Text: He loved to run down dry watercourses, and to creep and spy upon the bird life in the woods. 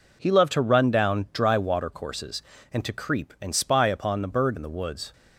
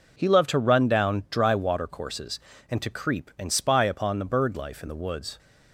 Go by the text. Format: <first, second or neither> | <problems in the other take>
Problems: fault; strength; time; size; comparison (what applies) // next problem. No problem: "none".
second | skips "life"; at 4.5 s